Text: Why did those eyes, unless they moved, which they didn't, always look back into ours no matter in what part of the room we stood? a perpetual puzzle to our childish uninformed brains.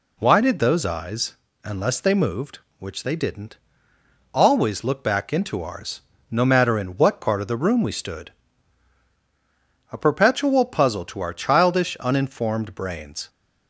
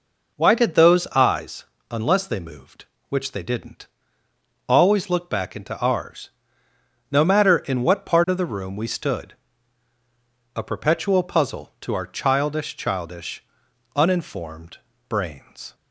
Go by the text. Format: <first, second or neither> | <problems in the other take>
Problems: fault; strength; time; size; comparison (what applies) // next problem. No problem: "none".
first | pauses between "ours" and "no"; noticeable; at 6.2 s; 0.80 s long; slight in the first // says "childish" twice; at 12.7 s // pauses between "uninformed" and "brains"; slight; at 14.7 s; 0.30 s long